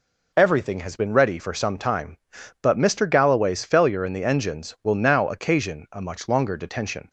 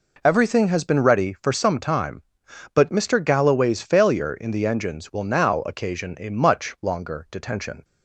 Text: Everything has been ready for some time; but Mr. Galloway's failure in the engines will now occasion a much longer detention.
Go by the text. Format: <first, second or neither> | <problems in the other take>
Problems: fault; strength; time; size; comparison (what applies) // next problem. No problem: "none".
neither | none